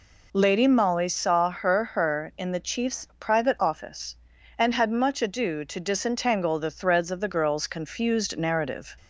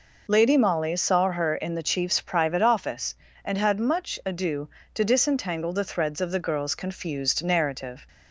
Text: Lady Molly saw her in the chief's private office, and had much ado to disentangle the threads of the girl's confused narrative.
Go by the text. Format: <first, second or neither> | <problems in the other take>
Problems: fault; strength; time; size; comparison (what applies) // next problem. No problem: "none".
second | says "her" twice; at 1.8 s